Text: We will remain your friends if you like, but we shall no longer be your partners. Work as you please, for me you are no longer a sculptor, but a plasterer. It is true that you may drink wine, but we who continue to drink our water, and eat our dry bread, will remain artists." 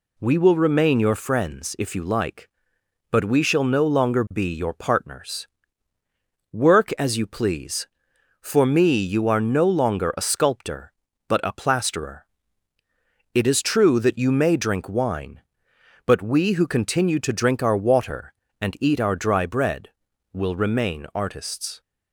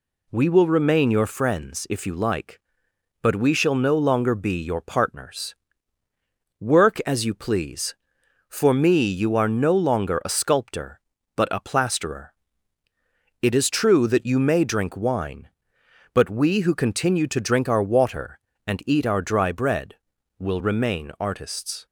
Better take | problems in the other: neither | none

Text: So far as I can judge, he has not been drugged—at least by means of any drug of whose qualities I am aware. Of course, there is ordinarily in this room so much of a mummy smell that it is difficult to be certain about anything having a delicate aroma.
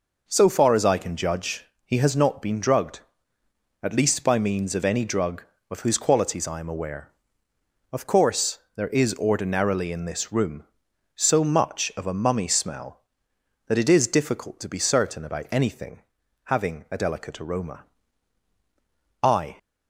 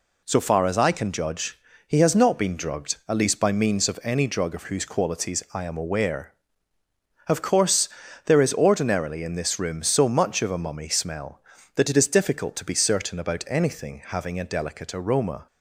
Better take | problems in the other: second | pauses between "anything" and "having"; at 16.0 s; 0.44 s long // goes on to say "I"; slight; from 19.2 s on; 0.34 s long

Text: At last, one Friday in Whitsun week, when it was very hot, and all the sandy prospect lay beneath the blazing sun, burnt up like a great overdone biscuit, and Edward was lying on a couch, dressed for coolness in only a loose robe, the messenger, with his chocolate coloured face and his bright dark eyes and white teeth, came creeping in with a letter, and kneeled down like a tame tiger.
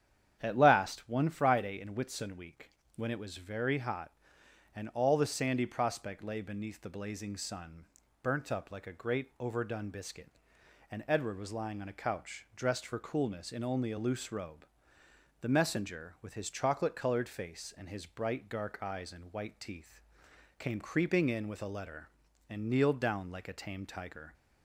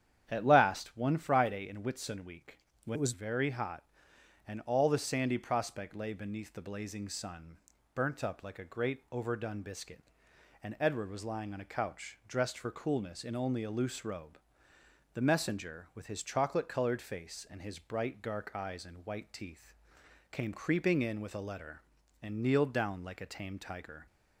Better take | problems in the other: first | starts louder than the rest; strong; until 1.2 s; 9 dB; strong in the first // changes voice from "it" to "was"; from 2.9 to 3.1 s; 0.2 s long

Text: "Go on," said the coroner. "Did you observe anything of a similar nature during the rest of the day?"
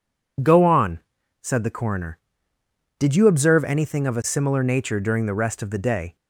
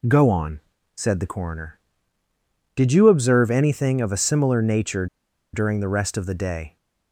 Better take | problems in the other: first | pauses between "nature" and "during"; noticeable; at 5.0 s; 0.47 s long

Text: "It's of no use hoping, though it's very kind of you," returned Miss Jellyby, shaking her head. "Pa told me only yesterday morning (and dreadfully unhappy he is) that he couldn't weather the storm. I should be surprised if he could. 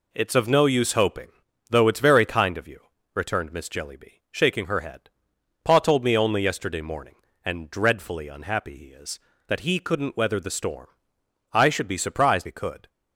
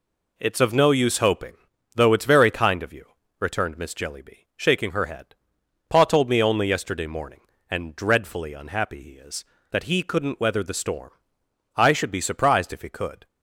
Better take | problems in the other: second | skips "if"; at 12.4 s

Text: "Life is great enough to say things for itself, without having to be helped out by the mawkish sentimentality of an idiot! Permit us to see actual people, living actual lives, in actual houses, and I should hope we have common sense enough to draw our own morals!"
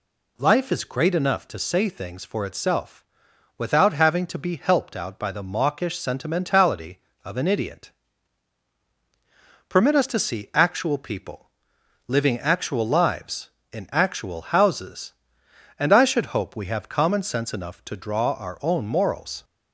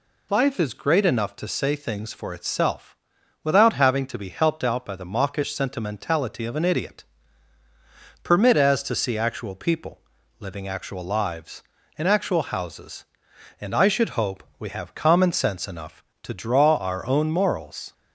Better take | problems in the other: first | says "as" for "us"; at 8.5 s // pauses between "hope" and "we"; slight; at 14.4 s; 0.16 s long

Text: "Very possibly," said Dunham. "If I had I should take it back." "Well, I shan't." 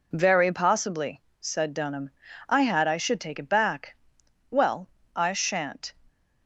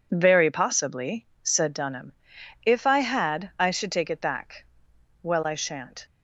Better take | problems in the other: second | skips "If"; at 2.2 s

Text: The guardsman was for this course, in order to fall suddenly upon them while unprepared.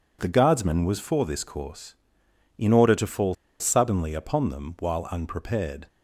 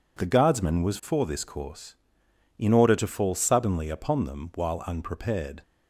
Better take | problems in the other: second | pauses between "fall" and "suddenly"; slight; at 3.3 s; 0.26 s long

